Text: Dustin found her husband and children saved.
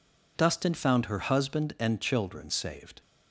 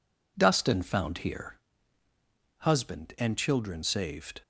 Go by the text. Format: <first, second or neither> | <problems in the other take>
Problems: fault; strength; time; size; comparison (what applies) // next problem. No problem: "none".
first | says "here" for "her"; at 1.1 s